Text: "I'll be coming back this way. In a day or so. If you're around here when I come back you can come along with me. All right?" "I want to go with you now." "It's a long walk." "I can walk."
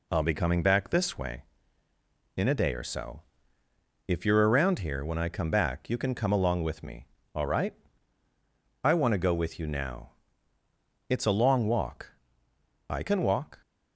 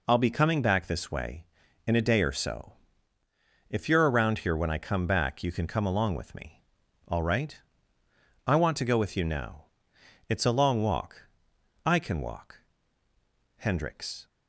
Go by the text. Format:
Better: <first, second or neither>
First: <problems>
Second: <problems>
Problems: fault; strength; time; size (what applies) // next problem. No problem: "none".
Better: first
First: none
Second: goes on to say "Hendricks"; noticeable; from 13.5 s on; 0.70 s long